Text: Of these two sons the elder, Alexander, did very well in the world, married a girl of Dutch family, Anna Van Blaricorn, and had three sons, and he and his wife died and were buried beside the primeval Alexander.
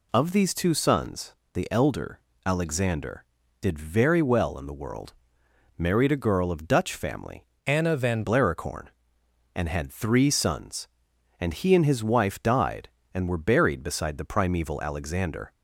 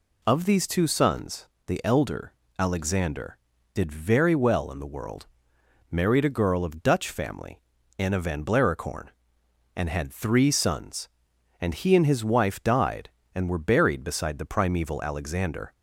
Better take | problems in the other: second | pauses between "sons" and "the"; slight; at 1.3 s; 0.20 s long; slight in the second // changes voice from "Anna" to "Van"; from 7.6 to 8.2 s; 0.6 s long

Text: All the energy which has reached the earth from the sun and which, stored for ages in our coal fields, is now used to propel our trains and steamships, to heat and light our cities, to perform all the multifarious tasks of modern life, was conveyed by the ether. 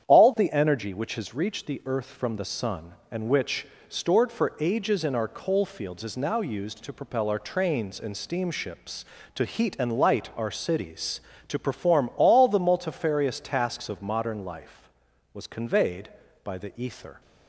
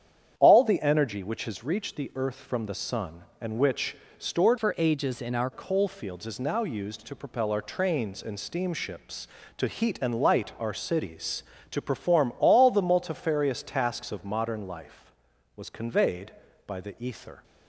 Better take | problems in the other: first | starts louder than the rest; strong; until 1.3 s; 8.5 dB; strong in the first // changes voice from "for" to "our"; from 4.5 to 5.5 s; 1.0 s long

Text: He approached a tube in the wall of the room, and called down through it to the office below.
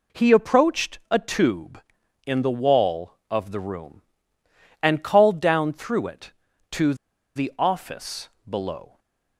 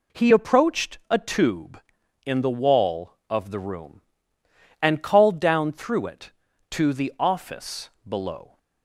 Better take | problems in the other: second | pauses between "to" and "the"; at 6.9 s; 0.41 s long // pauses between "office" and "below"; slight; at 8.2 s; 0.20 s long; slight in the second // stays silent after the last word; slight; from 8.8 s on; 0.5 s long

